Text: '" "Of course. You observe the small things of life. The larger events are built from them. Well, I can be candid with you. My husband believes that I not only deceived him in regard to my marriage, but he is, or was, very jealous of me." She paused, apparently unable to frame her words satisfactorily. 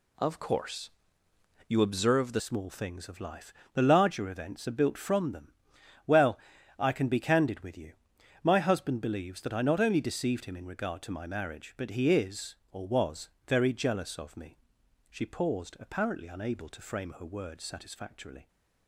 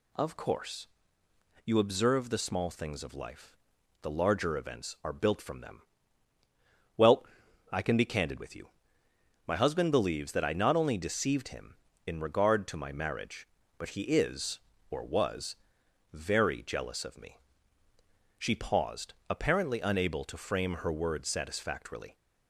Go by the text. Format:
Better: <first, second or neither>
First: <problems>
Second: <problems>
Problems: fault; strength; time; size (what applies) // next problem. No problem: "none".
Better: second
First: changes voice at "small"; from 2.3 s on; 16.1 s long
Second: none